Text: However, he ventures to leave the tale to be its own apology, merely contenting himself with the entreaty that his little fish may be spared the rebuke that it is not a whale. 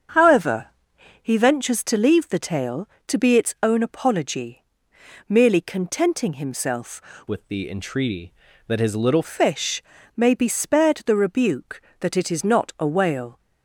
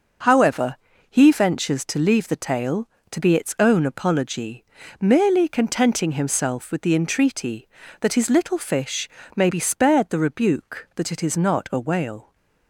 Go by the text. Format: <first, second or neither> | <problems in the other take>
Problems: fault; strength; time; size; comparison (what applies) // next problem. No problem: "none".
second | starts louder than the rest; strong; until 1.6 s; 7.5 dB // changes voice from "with" to "little"; from 7.2 to 9.2 s; 2.0 s long // pauses between "fish" and "may"; slight; at 9.8 s; 0.34 s long; slight in the second